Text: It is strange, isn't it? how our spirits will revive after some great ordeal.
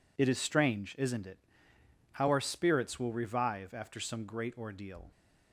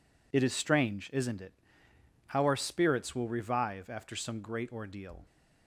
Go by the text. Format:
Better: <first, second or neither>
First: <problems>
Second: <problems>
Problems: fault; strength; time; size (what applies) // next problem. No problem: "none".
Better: neither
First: none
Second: none